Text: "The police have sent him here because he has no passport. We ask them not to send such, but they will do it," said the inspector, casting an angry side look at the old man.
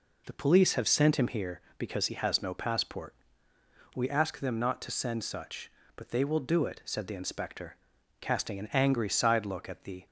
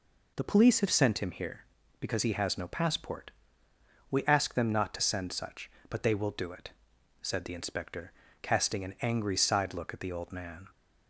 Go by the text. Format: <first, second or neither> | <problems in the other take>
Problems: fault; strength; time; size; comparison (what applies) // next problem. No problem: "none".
second | stops before "old man"; at 10.0 s